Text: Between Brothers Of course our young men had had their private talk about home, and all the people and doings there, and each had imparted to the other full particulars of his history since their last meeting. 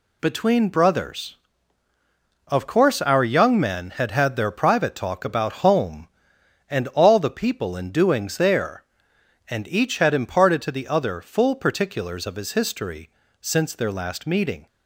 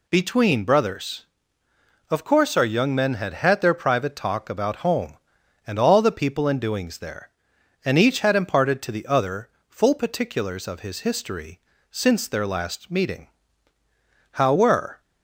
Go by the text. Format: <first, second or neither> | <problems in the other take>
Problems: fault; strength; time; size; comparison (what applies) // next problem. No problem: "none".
first | pauses between "other" and "full"; slight; at 9.4 s; 0.18 s long // pauses between "history" and "since"; slight; at 11.5 s; 0.30 s long; slight in the first // goes on to say "How were"; noticeable; from 14.3 s on; 0.68 s long